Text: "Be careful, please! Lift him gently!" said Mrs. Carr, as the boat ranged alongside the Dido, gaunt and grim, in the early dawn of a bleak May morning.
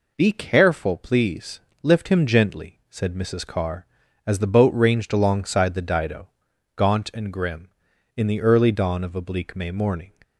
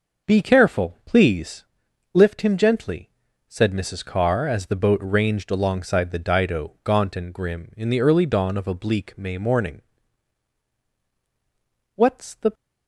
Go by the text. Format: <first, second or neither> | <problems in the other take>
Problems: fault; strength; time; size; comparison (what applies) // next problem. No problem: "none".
first | goes on to say "What's the"; from 11.9 s on; 0.58 s long